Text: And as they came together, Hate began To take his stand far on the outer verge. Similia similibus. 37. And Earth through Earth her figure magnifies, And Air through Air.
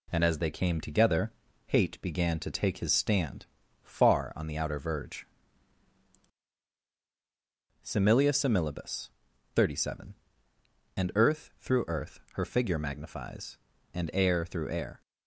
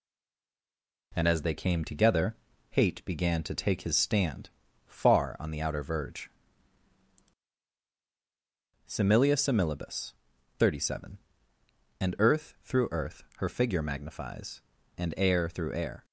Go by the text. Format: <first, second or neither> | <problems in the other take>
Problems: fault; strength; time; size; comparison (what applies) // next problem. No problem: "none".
first | stays silent before the first word; until 1.1 s; 1.1 s long // pauses between "stand" and "far"; at 4.4 s; 0.38 s long; also in the first